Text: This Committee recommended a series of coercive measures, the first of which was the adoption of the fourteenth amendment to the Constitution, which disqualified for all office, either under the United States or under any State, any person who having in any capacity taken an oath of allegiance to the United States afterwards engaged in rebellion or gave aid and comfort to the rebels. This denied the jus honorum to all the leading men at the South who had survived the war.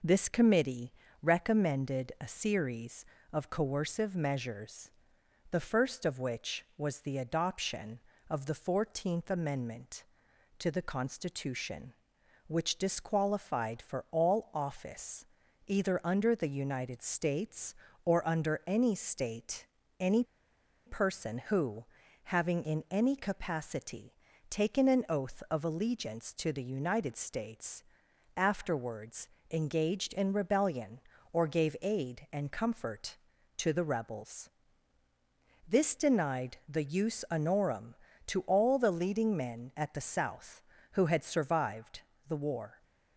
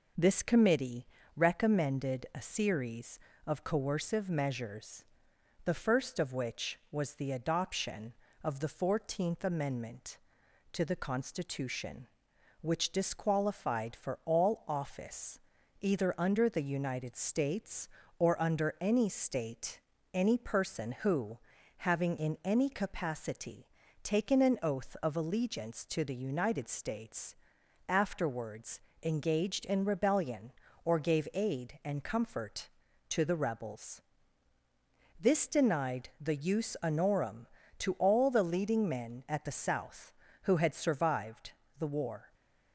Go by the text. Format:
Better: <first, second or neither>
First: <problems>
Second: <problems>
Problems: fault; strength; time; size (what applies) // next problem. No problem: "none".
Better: second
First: pauses between "Committee" and "recommended"; slight; at 0.9 s; 0.30 s long // pauses between "any" and "person"; noticeable; at 20.2 s; 0.61 s long // pauses between "who" and "having"; at 21.8 s; 0.44 s long // pauses between "capacity" and "taken"; slight; at 24.1 s; 0.36 s long // pauses between "States" and "afterwards"; noticeable; at 27.8 s; 0.54 s long // pauses between "afterwards" and "engaged"; slight; at 29.2 s; 0.24 s long // pauses between "survived" and "the"; slight; at 42.0 s; 0.26 s long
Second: pauses between "Committee" and "recommended"; slight; at 1.0 s; 0.30 s long // pauses between "who" and "having"; at 21.3 s; 0.44 s long // pauses between "capacity" and "taken"; slight; at 23.6 s; 0.36 s long // pauses between "States" and "afterwards"; noticeable; at 27.3 s; 0.54 s long // pauses between "afterwards" and "engaged"; slight; at 28.7 s; 0.24 s long // pauses between "survived" and "the"; slight; at 41.5 s; 0.26 s long